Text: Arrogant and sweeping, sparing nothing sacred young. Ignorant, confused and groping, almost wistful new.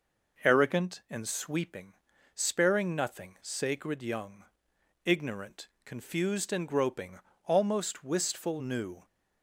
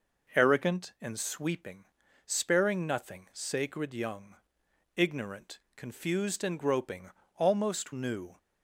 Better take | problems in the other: first | skips "wistful"; at 7.9 s

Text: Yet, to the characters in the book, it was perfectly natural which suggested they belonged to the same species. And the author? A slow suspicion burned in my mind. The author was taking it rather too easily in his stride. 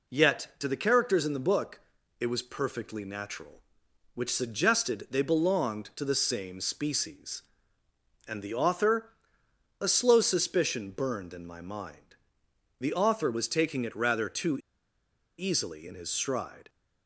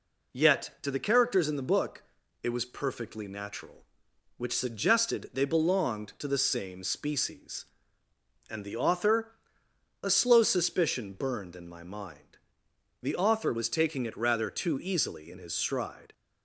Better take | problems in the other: second | pauses between "too" and "easily"; noticeable; at 14.5 s; 0.80 s long

